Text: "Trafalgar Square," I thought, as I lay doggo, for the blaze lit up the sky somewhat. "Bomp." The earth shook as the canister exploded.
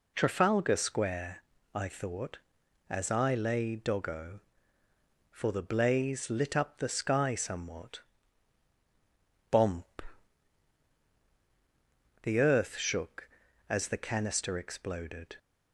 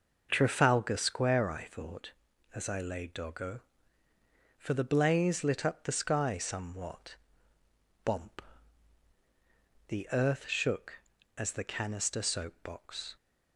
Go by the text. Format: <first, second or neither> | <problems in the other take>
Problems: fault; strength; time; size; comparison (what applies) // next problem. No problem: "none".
first | says "soapbox" for "exploded"; at 12.2 s